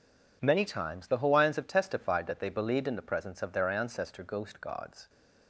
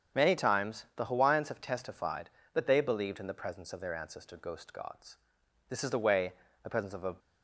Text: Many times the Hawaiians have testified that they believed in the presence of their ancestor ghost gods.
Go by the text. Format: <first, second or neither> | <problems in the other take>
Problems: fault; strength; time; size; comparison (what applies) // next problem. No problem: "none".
first | starts louder than the rest; strong; until 1.2 s; 7.5 dB // goes on to say "This is the way the presence of a"; from 5.6 s on; 1.4 s long